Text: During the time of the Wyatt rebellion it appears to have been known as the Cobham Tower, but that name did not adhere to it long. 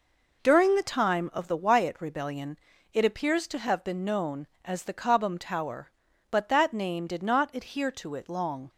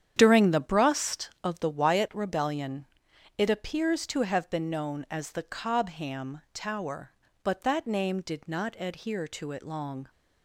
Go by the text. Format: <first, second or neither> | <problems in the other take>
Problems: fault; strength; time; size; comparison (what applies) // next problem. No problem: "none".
first | starts louder than the rest; strong; until 1.1 s; 9 dB // says "brust" for "time"; at 0.5 s // pauses between "rebellion" and "it"; noticeable; at 2.8 s; 0.52 s long; slight in the first